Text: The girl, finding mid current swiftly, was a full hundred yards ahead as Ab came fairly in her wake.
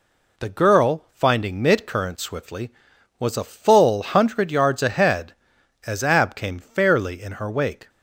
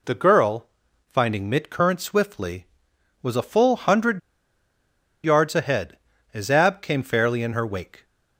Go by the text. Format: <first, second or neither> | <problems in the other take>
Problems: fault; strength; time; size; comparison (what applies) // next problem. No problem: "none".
first | pauses between "hundred" and "yards"; at 4.1 s; 1.0 s long